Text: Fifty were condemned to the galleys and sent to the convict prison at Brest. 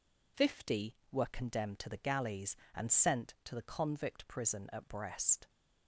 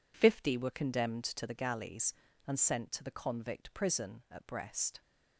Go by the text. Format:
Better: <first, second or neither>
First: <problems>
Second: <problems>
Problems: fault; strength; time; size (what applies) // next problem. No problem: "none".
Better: neither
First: none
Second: none